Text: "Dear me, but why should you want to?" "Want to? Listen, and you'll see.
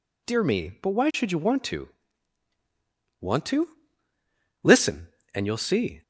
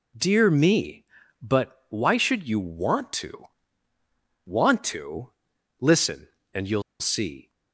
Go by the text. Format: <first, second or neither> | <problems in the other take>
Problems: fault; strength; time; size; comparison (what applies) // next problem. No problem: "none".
first | pauses between "you'll" and "see"; slight; at 6.8 s; 0.17 s long